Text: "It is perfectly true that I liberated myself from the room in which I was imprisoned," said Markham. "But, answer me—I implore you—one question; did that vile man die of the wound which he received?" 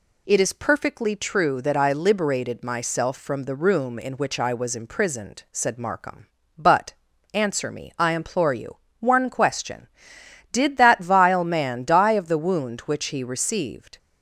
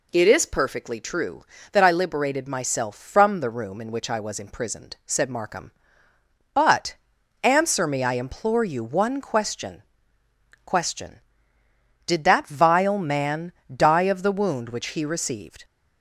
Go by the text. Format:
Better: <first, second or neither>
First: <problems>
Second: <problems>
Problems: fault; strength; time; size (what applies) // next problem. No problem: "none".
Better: first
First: none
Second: says "question" twice; at 10.6 s // pauses between "man" and "die"; slight; at 13.5 s; 0.24 s long